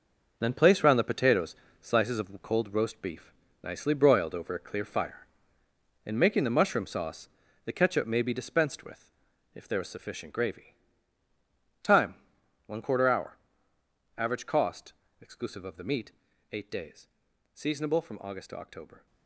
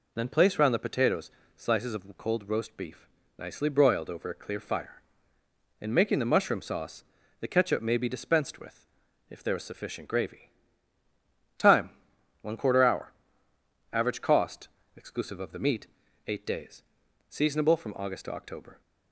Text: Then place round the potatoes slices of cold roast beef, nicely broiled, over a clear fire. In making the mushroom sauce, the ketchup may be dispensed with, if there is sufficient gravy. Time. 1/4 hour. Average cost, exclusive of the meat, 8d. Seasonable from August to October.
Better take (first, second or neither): second